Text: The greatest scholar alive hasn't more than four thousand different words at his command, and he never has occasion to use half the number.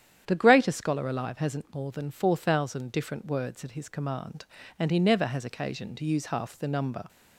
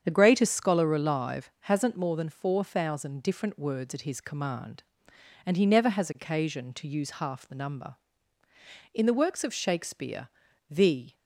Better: first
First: starts louder than the rest; strong; until 1.2 s; 9.5 dB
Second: starts louder than the rest; strong; until 1.0 s; 8 dB // goes on to say "In the works of Shakespeare the"; strong; from 8.9 s on; 2.2 s long

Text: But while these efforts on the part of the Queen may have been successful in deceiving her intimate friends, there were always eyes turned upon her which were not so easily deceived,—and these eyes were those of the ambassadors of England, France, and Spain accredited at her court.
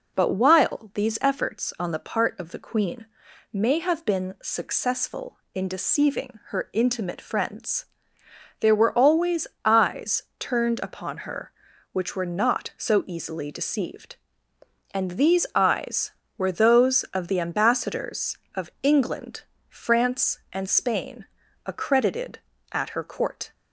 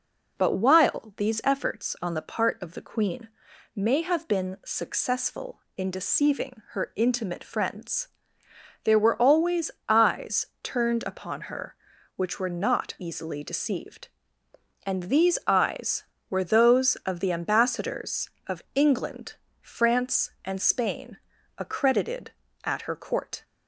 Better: first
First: pauses between "Queen" and "may"; noticeable; at 3.0 s; 0.48 s long // pauses between "always" and "eyes"; slight; at 9.4 s; 0.18 s long // pauses between "Spain" and "accredited"; at 21.2 s; 0.40 s long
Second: pauses between "Queen" and "may"; noticeable; at 3.2 s; 0.48 s long // pauses between "always" and "eyes"; slight; at 9.6 s; 0.18 s long // skips "so"; at 12.9 s // pauses between "Spain" and "accredited"; at 21.1 s; 0.40 s long

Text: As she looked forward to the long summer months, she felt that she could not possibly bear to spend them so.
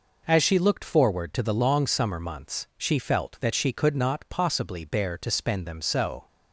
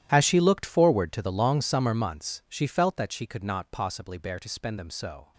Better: first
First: none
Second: gets quieter; strong; throughout; 18 dB

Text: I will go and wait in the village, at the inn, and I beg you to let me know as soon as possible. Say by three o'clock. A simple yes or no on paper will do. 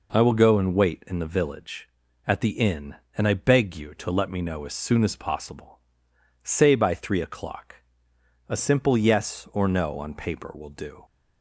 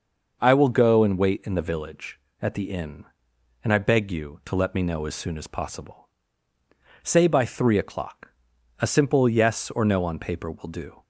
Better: neither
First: none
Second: none

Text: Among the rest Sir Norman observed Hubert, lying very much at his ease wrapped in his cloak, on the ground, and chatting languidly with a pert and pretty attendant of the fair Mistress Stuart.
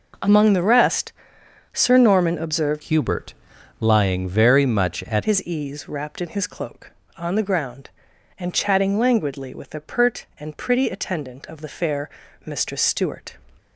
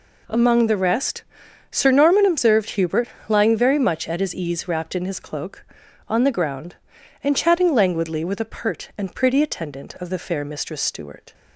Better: second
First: pauses between "rest" and "Sir"; noticeable; at 1.1 s; 0.62 s long // changes voice from "Hubert" to "at"; from 2.8 to 5.2 s; 2.4 s long // pauses between "fair" and "Mistress"; slight; at 12.0 s; 0.34 s long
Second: pauses between "rest" and "Sir"; noticeable; at 1.2 s; 0.48 s long

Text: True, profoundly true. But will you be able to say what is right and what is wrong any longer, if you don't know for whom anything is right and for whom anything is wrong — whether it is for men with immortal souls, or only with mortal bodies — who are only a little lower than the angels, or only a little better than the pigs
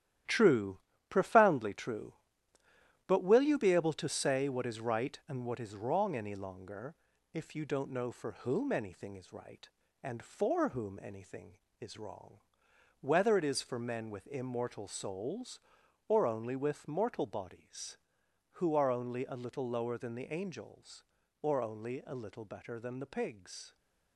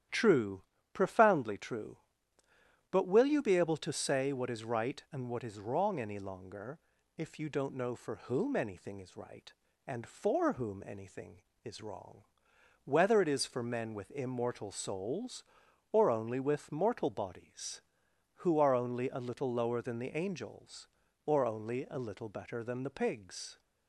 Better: second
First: gets quieter; strong; throughout; 8 dB // starts louder than the rest; strong; until 1.5 s; 12 dB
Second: starts louder than the rest; strong; until 1.3 s; 11 dB

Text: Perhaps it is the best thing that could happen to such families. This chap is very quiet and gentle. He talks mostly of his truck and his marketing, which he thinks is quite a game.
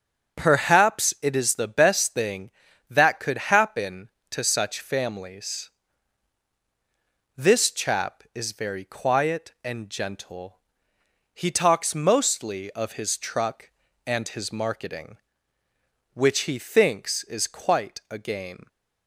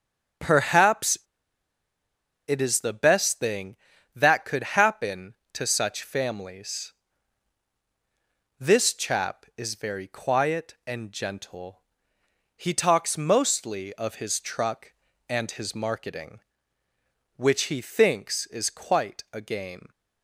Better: first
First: starts louder than the rest; until 1.4 s; 7 dB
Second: starts louder than the rest; until 2.7 s; 7 dB // pauses between "Perhaps" and "it"; strong; at 1.1 s; 1.3 s long

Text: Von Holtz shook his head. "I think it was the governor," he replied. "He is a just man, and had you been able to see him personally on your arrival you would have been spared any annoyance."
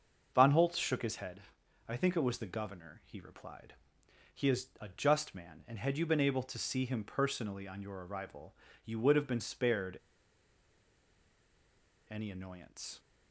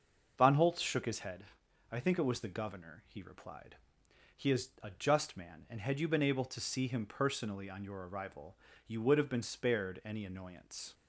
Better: second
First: starts louder than the rest; until 1.3 s; 6.5 dB // pauses between "arrival" and "you"; slight; at 8.5 s; 0.30 s long // pauses between "spared" and "any"; strong; at 9.9 s; 2.1 s long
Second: starts louder than the rest; until 1.3 s; 6.5 dB // pauses between "arrival" and "you"; slight; at 8.5 s; 0.30 s long

